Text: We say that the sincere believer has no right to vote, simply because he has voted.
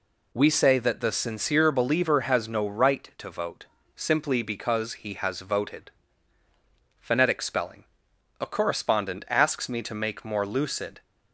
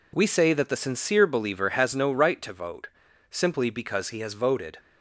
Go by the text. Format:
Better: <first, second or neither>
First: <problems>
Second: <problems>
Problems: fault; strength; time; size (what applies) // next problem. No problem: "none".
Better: second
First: goes on to say "PHONETIC SPELLING A correspondent asks me to make more lucid"; strong; from 7.0 s on; 4.0 s long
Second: none